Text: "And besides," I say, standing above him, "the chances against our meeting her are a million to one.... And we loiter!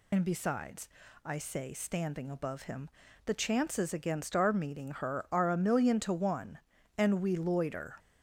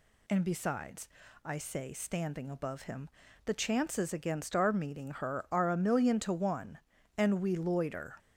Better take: second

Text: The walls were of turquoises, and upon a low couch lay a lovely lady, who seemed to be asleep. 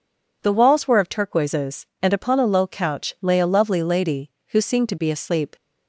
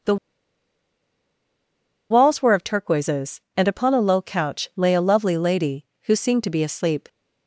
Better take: first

